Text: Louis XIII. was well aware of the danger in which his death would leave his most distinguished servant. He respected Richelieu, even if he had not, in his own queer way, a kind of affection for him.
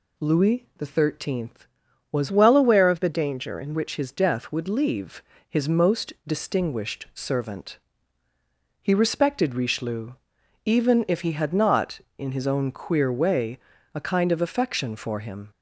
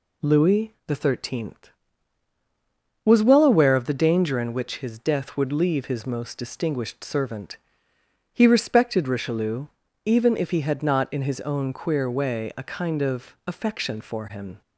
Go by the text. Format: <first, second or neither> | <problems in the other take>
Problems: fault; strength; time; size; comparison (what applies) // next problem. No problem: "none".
second | changes voice from "well" to "in"; from 2.3 to 3.7 s; 1.4 s long // pauses between "leave" and "his"; slight; at 5.2 s; 0.28 s long